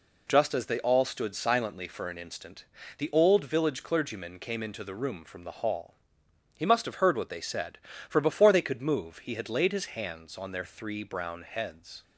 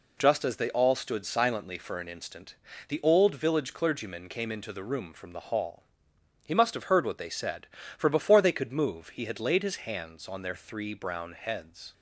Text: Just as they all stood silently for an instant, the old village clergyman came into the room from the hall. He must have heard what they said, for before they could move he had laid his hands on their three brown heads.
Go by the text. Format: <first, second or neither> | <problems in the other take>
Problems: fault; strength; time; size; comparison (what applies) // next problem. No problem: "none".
neither | none